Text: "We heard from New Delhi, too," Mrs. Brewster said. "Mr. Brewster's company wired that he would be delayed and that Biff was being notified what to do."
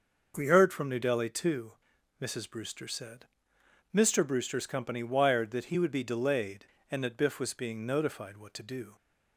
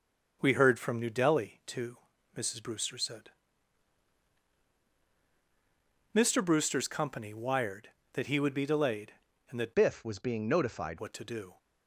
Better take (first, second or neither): first